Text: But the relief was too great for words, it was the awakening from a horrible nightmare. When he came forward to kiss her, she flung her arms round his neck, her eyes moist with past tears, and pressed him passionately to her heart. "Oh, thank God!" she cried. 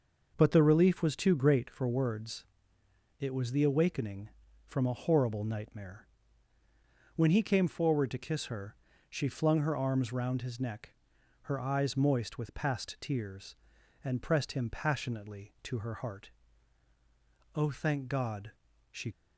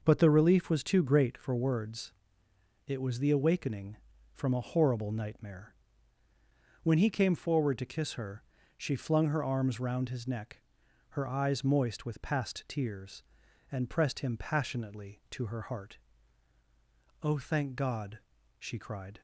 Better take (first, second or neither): second